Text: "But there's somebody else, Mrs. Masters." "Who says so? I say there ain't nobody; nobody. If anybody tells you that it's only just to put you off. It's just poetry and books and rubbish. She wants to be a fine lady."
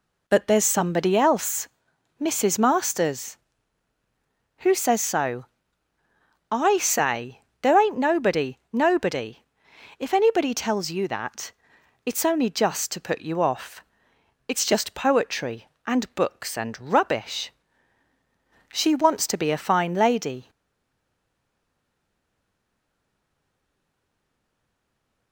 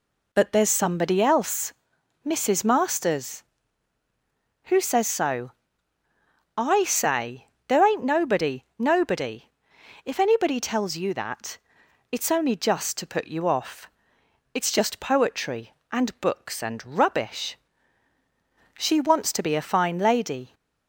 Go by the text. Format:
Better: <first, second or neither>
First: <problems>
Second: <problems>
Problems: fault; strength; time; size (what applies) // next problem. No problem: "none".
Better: second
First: pauses between "say" and "there"; slight; at 7.4 s; 0.20 s long // pauses between "that" and "it's"; noticeable; at 11.5 s; 0.52 s long // stays silent after the last word; strong; from 20.4 s on; 4.9 s long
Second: pauses between "say" and "there"; slight; at 7.4 s; 0.20 s long // pauses between "that" and "it's"; noticeable; at 11.5 s; 0.52 s long